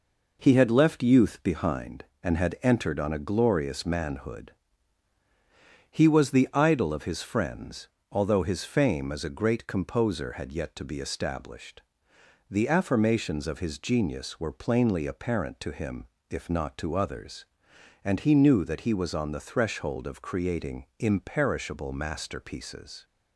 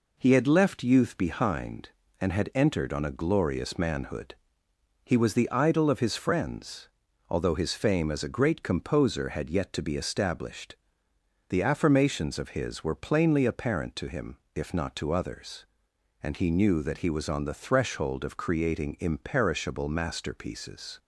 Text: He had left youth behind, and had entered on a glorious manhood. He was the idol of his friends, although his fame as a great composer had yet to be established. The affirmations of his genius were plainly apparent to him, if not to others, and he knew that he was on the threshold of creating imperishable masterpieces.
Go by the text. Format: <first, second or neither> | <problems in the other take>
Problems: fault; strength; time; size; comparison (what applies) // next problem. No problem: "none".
first | skips "genius"; at 12.8 s